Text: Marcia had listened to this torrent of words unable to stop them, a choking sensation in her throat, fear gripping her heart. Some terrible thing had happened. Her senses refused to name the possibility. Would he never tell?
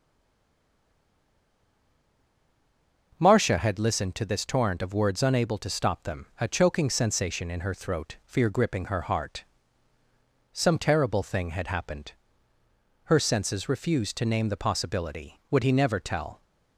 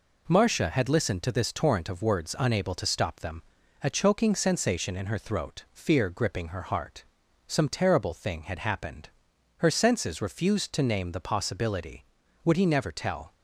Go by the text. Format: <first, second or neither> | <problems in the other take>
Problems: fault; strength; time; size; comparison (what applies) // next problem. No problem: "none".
second | stays silent before the first word; strong; until 3.1 s; 3.1 s long